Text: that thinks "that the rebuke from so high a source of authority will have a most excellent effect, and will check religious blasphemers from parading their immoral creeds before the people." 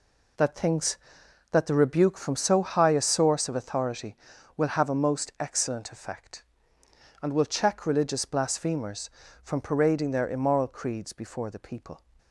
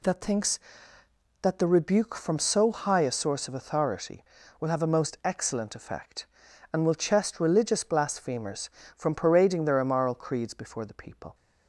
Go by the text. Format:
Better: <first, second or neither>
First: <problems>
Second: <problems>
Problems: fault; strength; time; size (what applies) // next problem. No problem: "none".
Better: first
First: none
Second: says "chest" for "check"; at 6.9 s